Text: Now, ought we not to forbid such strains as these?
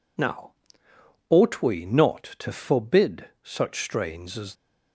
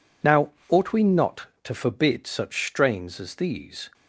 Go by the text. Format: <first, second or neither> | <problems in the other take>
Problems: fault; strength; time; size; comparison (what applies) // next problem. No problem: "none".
second | stops before "these"; at 4.5 s